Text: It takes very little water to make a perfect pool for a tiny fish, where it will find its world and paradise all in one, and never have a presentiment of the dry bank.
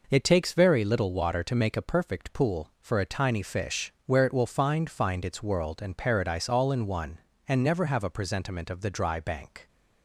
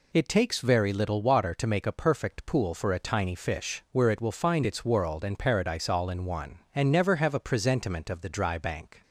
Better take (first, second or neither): second